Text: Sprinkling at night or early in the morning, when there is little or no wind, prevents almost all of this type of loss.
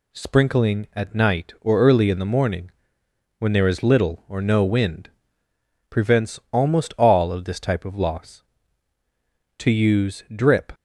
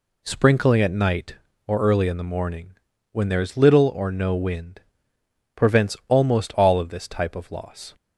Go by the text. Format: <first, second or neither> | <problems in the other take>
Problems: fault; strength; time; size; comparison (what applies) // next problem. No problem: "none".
second | goes on to say "To use drip"; noticeable; from 9.5 s on; 1.1 s long